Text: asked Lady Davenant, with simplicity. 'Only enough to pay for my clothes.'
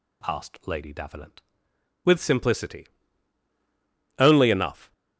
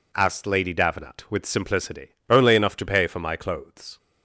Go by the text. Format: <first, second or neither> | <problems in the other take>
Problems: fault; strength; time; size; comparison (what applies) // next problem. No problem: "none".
second | stops before "to pay for my clothes"; at 4.9 s